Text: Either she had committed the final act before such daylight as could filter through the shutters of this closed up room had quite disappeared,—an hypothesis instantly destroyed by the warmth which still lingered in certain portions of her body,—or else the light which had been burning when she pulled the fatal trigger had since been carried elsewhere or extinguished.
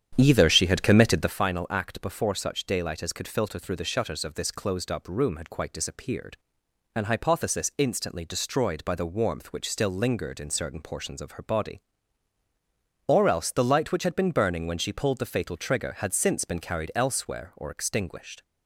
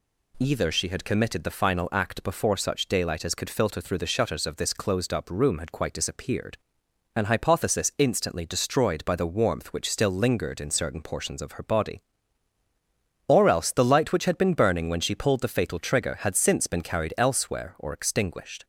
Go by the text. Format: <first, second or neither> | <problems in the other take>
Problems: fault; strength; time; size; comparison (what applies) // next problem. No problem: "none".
second | starts louder than the rest; strong; until 1.4 s; 9 dB